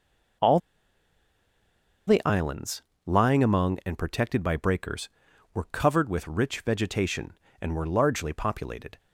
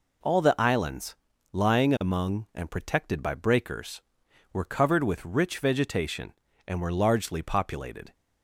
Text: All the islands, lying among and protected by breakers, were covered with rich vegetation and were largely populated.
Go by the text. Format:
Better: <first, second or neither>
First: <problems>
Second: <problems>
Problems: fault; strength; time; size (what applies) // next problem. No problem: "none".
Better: second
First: pauses between "All" and "the"; strong; at 0.6 s; 1.4 s long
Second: none